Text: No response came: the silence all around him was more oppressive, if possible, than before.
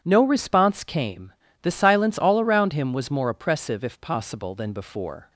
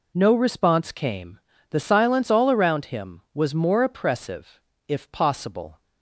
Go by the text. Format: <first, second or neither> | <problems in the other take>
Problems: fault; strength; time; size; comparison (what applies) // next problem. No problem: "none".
first | stops before "than before"; at 5.8 s